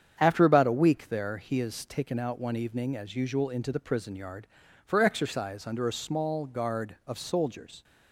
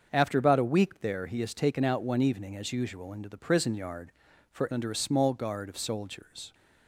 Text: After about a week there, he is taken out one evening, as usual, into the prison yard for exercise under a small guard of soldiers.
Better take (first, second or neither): first